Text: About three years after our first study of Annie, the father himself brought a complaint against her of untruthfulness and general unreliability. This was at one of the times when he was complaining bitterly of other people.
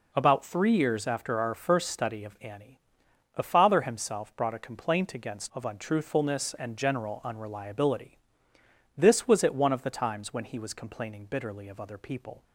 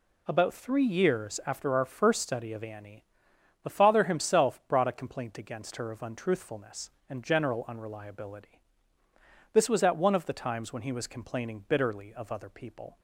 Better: second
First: skips "her"; at 5.5 s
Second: none

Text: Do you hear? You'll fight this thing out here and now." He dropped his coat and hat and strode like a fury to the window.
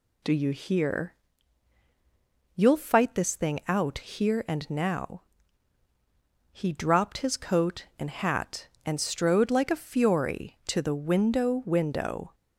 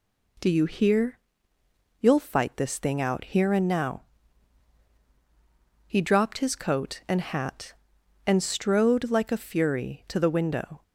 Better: second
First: says "window" twice; at 11.6 s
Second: none

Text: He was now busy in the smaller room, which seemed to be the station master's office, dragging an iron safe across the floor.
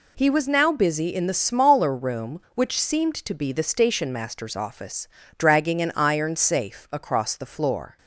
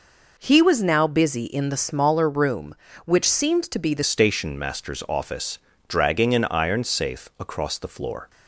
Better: first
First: none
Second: changes voice at "station"; from 4.0 s on; 4.2 s long

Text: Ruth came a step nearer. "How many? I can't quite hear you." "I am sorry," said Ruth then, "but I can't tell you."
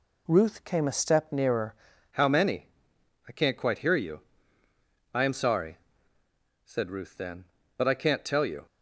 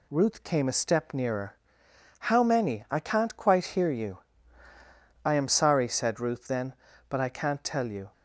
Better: second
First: changes voice at "How"; from 2.1 s on; 6.5 s long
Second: none

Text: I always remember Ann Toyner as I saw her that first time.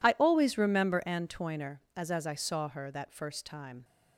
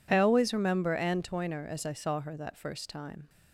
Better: second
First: says "as" twice; at 2.1 s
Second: none

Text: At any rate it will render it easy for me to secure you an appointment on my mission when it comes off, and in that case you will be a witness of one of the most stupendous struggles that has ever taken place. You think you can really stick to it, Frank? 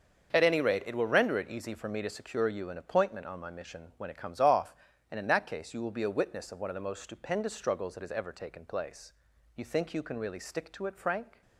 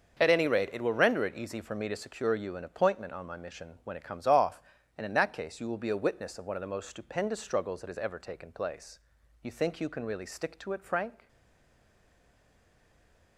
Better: first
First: starts louder than the rest; until 1.3 s; 6.5 dB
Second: starts louder than the rest; until 1.2 s; 6.5 dB // stays silent after the last word; from 11.2 s on; 2.1 s long

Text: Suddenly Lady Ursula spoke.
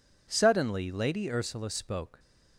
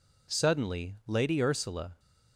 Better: first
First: none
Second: stops before "spoke"; at 1.9 s

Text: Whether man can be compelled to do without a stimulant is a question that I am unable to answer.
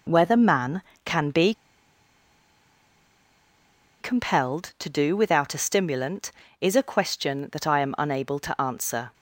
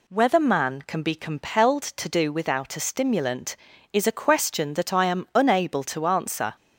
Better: second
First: pauses between "be" and "compelled"; strong; at 1.5 s; 2.4 s long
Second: none

